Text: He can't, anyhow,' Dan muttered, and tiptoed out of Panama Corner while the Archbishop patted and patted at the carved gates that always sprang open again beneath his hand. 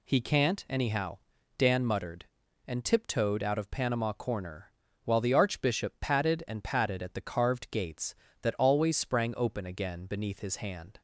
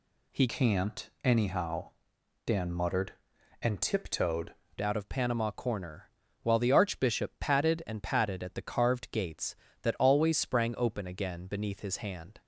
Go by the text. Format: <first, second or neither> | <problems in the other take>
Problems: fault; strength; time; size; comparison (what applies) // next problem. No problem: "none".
first | changes voice from "can't" to "tiptoed"; from 0.4 to 4.5 s; 4.1 s long // pauses between "Corner" and "while"; slight; at 6.0 s; 0.36 s long; slight in the first